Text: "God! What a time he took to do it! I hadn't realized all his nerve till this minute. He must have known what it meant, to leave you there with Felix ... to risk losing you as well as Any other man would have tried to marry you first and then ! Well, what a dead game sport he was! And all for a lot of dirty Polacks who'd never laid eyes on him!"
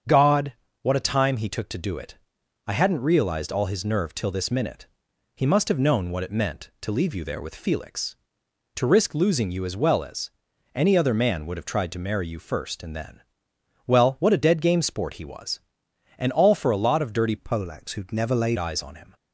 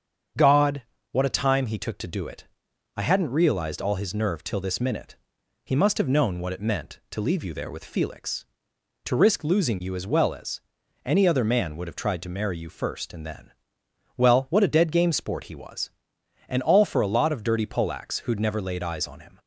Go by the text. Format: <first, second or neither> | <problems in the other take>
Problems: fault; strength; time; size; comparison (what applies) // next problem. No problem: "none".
second | starts louder than the rest; until 1.3 s; 7 dB; also in the second // pauses between "as" and "Any"; noticeable; at 10.2 s; 0.46 s long; noticeable in the second // changes voice from "Polacks" to "laid"; from 17.3 to 18.5 s; 1.2 s long